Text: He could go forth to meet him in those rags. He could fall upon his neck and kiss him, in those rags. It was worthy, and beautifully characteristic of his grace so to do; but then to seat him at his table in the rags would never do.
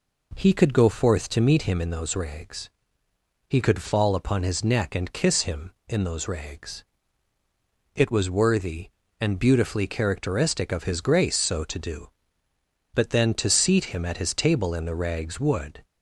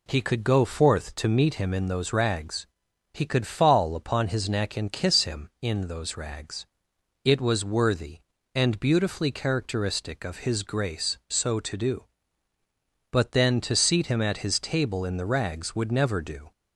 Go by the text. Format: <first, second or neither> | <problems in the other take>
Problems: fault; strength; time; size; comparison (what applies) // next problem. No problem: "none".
second | stops before "never do"; at 15.8 s